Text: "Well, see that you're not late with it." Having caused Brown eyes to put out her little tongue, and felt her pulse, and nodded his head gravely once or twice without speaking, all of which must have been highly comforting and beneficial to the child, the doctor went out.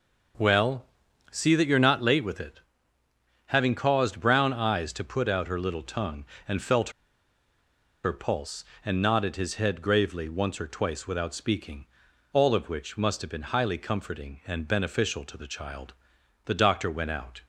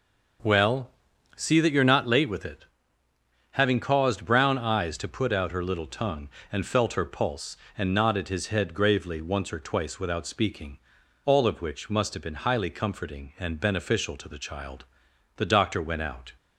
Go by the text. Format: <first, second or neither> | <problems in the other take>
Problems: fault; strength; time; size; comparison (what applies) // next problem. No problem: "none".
second | pauses between "felt" and "her"; at 6.8 s; 1.1 s long